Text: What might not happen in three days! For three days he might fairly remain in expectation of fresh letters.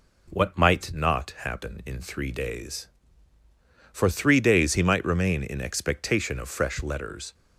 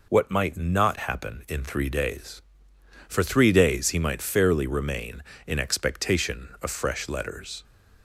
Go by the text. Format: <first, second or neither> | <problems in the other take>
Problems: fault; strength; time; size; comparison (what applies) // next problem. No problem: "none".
second | skips "fairly"; at 5.0 s